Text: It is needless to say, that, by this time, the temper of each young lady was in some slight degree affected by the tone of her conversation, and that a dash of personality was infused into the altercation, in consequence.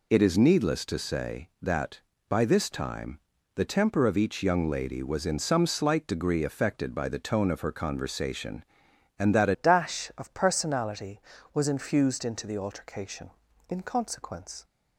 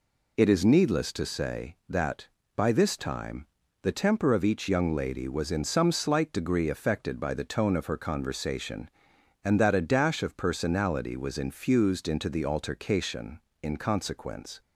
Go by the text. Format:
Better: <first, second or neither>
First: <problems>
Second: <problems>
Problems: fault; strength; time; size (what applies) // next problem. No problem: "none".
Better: second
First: changes voice at "dash"; from 9.5 s on; 5.1 s long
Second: none